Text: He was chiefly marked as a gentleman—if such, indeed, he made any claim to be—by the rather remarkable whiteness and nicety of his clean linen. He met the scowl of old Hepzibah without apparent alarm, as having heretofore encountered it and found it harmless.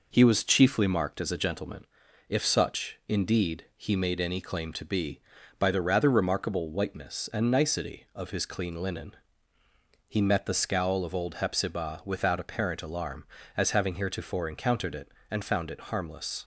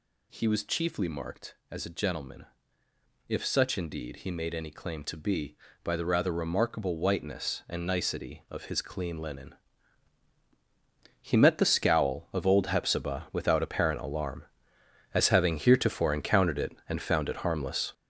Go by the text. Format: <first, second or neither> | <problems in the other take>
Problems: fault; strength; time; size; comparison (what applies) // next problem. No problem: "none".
first | gets louder; strong; throughout; 8 dB